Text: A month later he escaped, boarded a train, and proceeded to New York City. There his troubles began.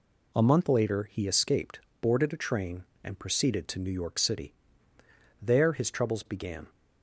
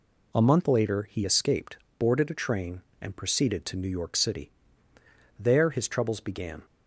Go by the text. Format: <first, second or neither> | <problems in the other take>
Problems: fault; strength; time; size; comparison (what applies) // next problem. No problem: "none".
neither | none